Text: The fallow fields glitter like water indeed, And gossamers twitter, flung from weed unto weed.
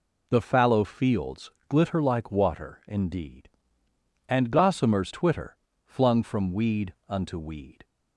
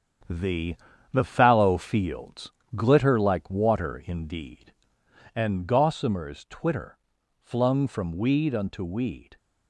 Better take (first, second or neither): first